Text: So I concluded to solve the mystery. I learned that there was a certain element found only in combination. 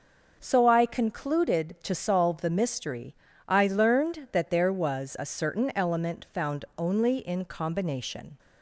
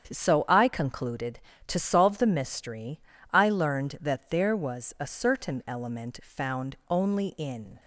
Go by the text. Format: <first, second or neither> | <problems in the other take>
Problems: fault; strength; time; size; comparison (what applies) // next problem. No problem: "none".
first | starts louder than the rest; strong; until 1.1 s; 8 dB // stops before "combination"; at 7.7 s